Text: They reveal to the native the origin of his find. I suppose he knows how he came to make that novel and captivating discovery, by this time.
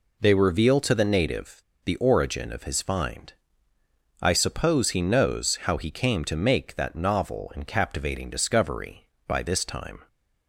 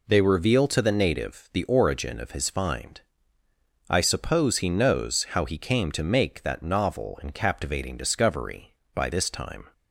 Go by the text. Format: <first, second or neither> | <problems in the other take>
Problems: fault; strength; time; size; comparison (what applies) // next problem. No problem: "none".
second | pauses between "native" and "the"; slight; at 1.6 s; 0.23 s long